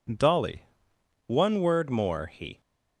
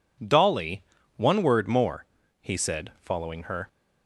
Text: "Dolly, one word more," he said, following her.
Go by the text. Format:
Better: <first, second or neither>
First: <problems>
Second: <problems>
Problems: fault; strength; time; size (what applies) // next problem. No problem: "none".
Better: second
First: stops before "said following her"; at 2.6 s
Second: none